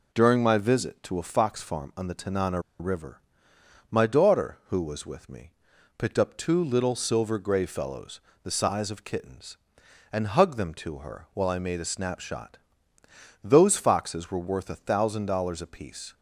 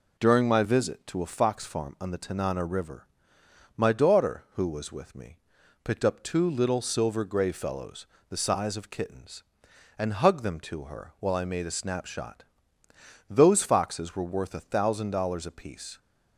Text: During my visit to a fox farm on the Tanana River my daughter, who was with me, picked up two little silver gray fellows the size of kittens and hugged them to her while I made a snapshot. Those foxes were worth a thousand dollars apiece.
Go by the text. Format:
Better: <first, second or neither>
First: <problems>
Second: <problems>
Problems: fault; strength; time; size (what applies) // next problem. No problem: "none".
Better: second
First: pauses between "Tanana" and "River"; slight; at 2.5 s; 0.19 s long // pauses between "River" and "my"; noticeable; at 3.1 s; 0.72 s long // pauses between "fellows" and "the"; slight; at 8.1 s; 0.24 s long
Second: pauses between "River" and "my"; noticeable; at 3.0 s; 0.72 s long // pauses between "fellows" and "the"; slight; at 8.0 s; 0.24 s long